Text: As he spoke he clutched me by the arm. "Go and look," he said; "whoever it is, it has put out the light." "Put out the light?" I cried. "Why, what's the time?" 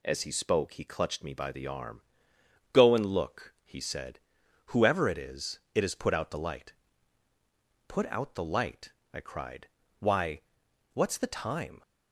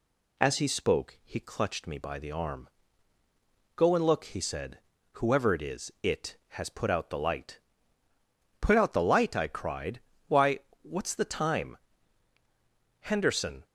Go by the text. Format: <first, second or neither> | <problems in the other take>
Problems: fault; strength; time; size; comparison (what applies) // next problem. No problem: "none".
first | goes on to say "Henderson"; noticeable; from 12.9 s on; 0.66 s long